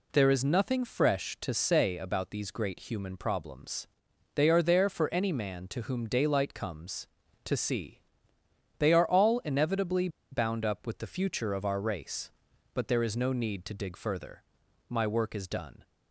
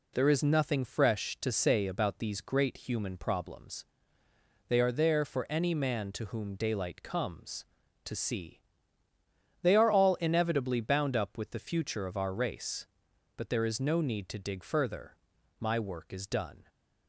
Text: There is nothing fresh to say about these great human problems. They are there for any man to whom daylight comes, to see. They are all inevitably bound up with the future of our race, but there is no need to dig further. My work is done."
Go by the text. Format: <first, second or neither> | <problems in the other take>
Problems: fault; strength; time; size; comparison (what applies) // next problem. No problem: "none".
second | pauses between "inevitably" and "bound"; slight; at 10.0 s; 0.23 s long